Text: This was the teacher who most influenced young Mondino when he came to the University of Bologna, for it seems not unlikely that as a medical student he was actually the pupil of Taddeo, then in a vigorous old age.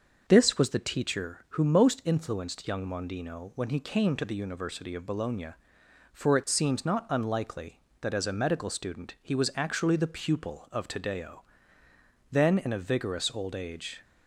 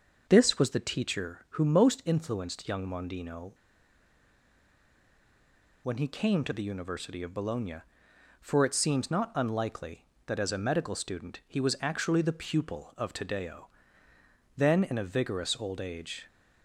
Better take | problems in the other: first | starts louder than the rest; noticeable; until 1.3 s; 6 dB; noticeable in the first // pauses between "Mondino" and "when"; strong; at 3.5 s; 2.3 s long

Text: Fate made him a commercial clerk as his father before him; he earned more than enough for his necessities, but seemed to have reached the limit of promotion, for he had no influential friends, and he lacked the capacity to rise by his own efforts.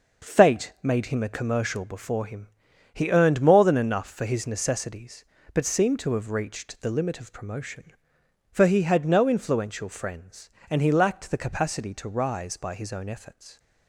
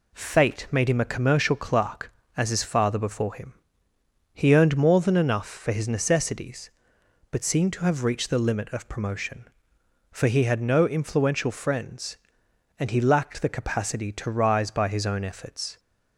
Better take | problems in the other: second | skips "clerk as his father"; at 1.8 s

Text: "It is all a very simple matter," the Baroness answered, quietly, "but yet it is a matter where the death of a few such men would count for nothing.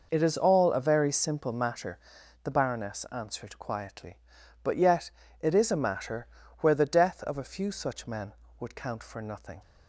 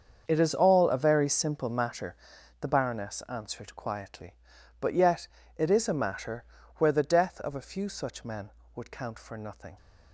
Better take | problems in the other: first | gets quieter; strong; throughout; 14 dB // pauses between "yet" and "it"; slight; at 5.2 s; 0.30 s long; slight in the first // pauses between "matter" and "where"; slight; at 6.4 s; 0.32 s long; slight in the first

